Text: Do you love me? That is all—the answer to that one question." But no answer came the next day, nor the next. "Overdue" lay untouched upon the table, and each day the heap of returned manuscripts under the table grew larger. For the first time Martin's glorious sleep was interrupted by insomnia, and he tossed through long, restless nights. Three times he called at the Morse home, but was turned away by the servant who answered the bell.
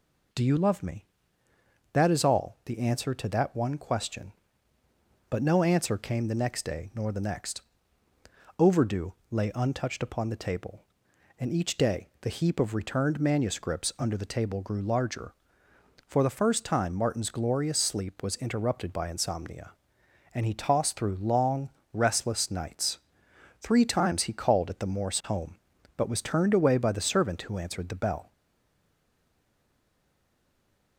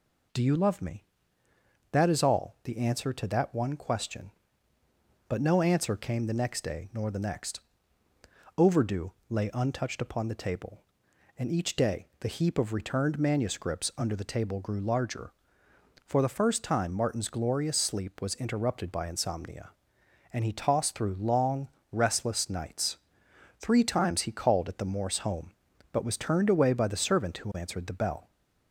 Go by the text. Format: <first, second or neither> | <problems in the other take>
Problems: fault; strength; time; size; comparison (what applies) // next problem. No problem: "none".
second | pauses between "Overdue" and "lay"; slight; at 9.1 s; 0.18 s long; slight in the second // stays silent after the last word; strong; from 28.3 s on; 2.6 s long